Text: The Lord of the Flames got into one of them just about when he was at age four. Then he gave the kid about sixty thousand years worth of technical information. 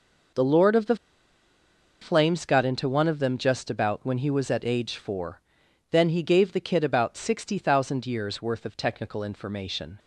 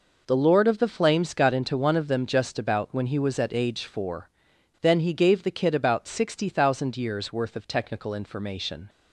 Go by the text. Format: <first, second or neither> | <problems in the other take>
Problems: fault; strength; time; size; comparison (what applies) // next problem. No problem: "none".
second | pauses between "the" and "Flames"; at 0.9 s; 1.0 s long